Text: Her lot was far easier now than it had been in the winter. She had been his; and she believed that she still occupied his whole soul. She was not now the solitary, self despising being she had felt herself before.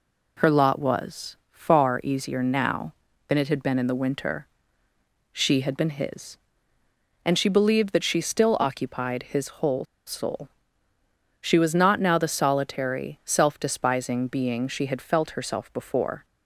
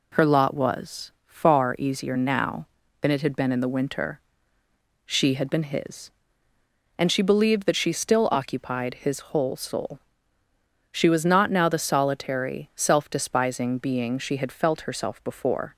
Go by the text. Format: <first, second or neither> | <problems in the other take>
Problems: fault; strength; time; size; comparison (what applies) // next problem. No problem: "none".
second | pauses between "whole" and "soul"; slight; at 9.8 s; 0.22 s long